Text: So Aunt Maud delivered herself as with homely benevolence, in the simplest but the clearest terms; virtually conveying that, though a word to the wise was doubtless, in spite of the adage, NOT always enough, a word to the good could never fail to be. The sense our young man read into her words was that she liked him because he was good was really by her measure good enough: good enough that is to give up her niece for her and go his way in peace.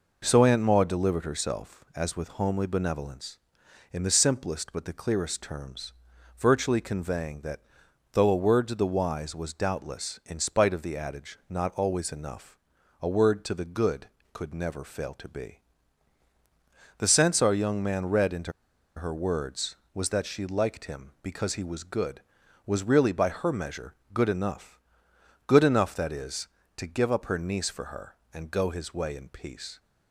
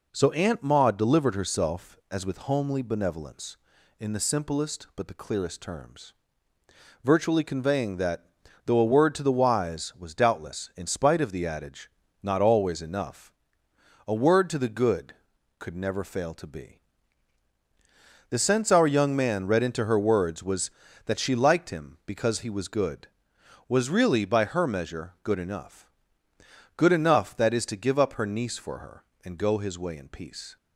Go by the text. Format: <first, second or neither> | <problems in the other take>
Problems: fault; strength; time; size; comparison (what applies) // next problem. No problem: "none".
second | pauses between "into" and "her"; at 18.5 s; 0.45 s long // pauses between "measure" and "good"; slight; at 23.9 s; 0.18 s long